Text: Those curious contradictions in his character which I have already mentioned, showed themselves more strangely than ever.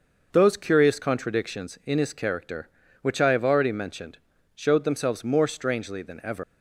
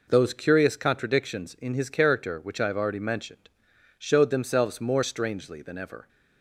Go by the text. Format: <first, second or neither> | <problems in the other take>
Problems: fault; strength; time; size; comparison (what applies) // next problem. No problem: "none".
second | leaves "ever" unfinished; at 6.4 s; 130 ms